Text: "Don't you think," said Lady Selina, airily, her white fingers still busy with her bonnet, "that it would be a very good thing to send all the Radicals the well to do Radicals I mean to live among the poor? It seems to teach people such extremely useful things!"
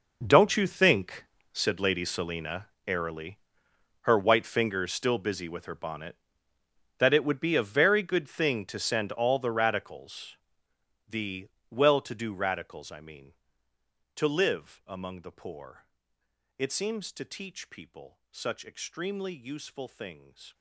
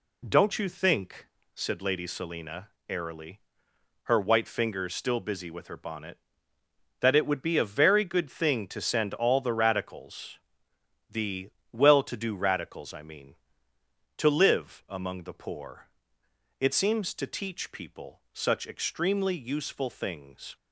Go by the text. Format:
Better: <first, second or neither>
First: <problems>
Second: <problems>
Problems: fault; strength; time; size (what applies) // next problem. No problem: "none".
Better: second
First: gets quieter; strong; throughout; 16 dB // pauses between "Radicals" and "the"; noticeable; at 10.3 s; 0.72 s long // pauses between "the" and "well"; slight; at 11.4 s; 0.22 s long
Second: pauses between "Radicals" and "the"; noticeable; at 10.3 s; 0.72 s long // pauses between "the" and "well"; slight; at 11.4 s; 0.22 s long